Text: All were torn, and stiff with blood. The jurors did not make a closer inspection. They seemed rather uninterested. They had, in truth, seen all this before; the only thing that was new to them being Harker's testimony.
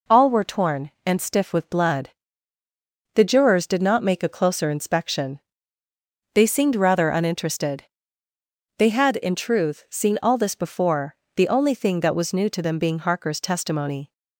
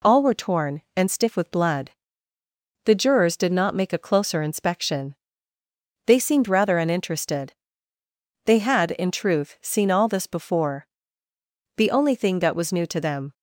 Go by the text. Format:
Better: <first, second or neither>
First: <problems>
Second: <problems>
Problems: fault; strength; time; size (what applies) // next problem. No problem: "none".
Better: first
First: none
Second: stops before "being Harker's testimony"; at 13.3 s